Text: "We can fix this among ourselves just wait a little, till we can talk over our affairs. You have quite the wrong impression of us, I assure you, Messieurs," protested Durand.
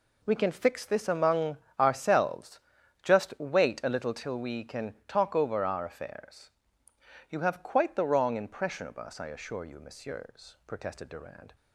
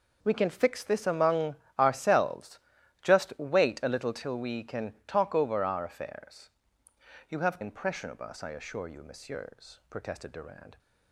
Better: first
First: pauses between "among" and "ourselves"; slight; at 1.5 s; 0.23 s long // pauses between "ourselves" and "just"; at 2.5 s; 0.42 s long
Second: pauses between "among" and "ourselves"; slight; at 1.5 s; 0.24 s long // pauses between "ourselves" and "just"; at 2.5 s; 0.42 s long // skips "quite the wrong"; at 7.6 s

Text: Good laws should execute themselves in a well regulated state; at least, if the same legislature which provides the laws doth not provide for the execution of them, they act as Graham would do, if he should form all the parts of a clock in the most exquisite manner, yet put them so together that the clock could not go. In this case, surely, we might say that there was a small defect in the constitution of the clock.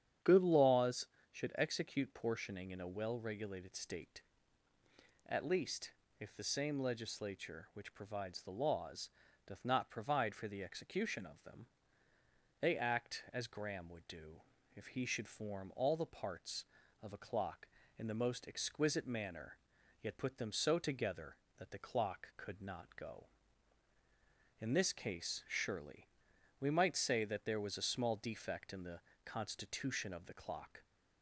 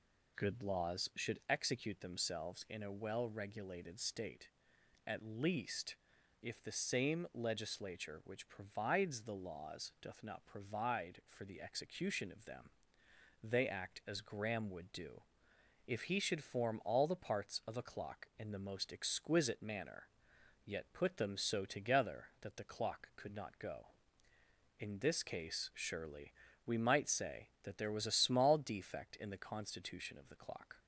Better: second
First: starts louder than the rest; strong; until 1.4 s; 9 dB // says "portioning" for "themselves"; at 2.1 s // pauses between "laws" and "doth"; at 9.0 s; 0.38 s long // pauses between "the" and "constitution"; slight; at 28.9 s; 0.24 s long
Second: none

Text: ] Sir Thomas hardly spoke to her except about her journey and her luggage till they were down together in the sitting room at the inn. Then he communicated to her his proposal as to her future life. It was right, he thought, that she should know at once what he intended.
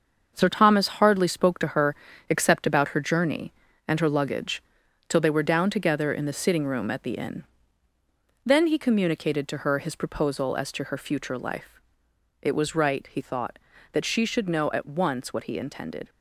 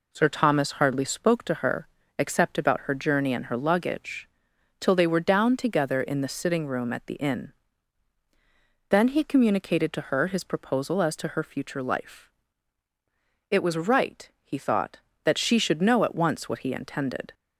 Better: second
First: gets quieter; strong; throughout; 8 dB // pauses between "her" and "except"; slight; at 1.9 s; 0.34 s long // pauses between "luggage" and "till"; noticeable; at 4.6 s; 0.46 s long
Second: pauses between "her" and "except"; slight; at 1.8 s; 0.30 s long // pauses between "luggage" and "till"; noticeable; at 4.2 s; 0.52 s long

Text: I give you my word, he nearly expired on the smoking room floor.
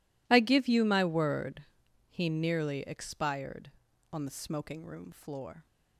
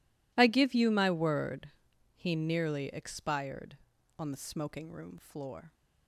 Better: neither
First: none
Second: none

